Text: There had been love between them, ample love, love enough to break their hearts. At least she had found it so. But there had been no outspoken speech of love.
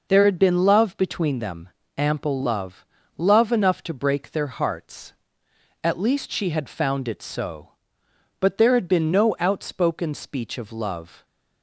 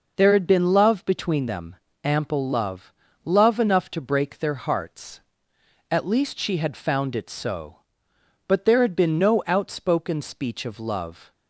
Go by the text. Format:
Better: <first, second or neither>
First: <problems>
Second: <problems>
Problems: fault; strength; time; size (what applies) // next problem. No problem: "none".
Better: neither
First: none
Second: none